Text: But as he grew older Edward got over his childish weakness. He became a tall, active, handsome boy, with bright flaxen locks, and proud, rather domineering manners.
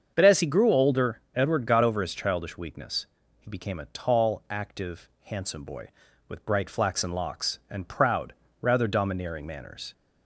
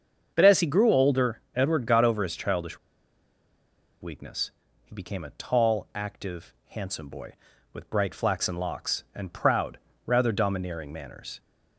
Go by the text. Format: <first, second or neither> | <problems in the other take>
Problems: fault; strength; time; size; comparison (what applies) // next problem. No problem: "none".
first | starts louder than the rest; until 1.3 s; 7 dB; also in the first // pauses between "older" and "Edward"; slight; at 1.3 s; 0.16 s long; slight in the first // pauses between "childish" and "weakness"; at 2.7 s; 1.2 s long